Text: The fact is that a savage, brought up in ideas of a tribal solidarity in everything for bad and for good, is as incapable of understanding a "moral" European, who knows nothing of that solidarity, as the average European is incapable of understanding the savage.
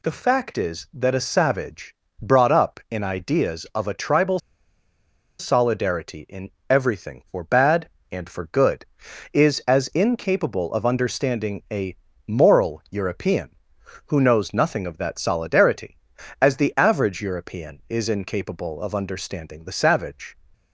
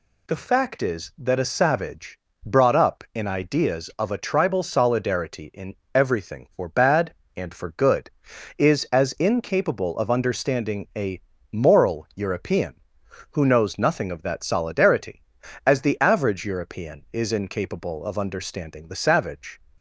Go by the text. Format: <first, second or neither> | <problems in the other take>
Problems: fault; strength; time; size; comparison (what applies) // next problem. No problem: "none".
second | pauses between "tribal" and "solidarity"; at 4.3 s; 0.99 s long // pauses between "in" and "everything"; slight; at 6.5 s; 0.18 s long; slight in the second // pauses between "a" and "moral"; slight; at 11.9 s; 0.30 s long; slight in the second